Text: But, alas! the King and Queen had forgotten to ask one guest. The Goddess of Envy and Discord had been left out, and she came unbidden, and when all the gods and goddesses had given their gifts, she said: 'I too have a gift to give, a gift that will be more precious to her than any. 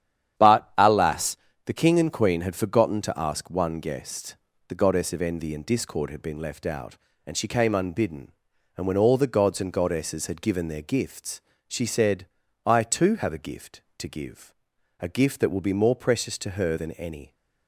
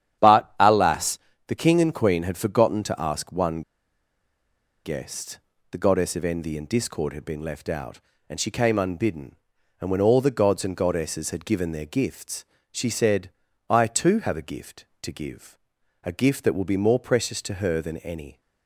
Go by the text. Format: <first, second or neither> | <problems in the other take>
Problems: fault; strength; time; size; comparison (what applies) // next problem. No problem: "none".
first | starts louder than the rest; strong; until 1.5 s; 10 dB; strong in the first // pauses between "one" and "guest"; at 3.6 s; 1.2 s long